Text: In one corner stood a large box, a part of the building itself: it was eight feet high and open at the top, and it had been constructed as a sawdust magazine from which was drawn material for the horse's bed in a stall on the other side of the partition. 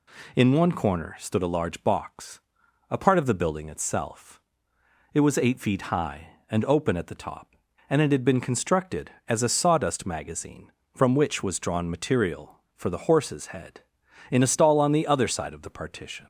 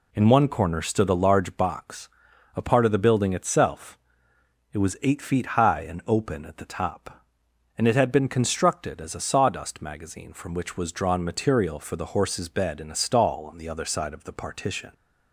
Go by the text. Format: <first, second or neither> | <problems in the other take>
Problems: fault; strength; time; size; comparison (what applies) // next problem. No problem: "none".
second | says "head" for "bed"; at 13.4 s